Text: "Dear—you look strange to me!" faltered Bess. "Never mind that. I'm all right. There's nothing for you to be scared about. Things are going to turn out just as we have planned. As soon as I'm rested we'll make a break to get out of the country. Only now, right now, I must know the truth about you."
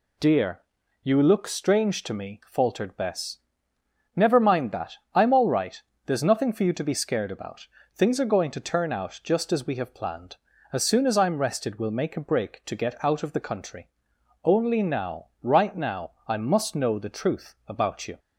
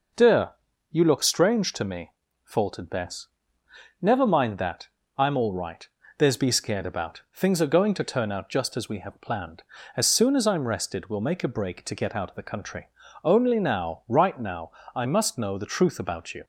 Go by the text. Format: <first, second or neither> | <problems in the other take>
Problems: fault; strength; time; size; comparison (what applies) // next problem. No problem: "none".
first | skips "nothing for you to"; at 6.3 s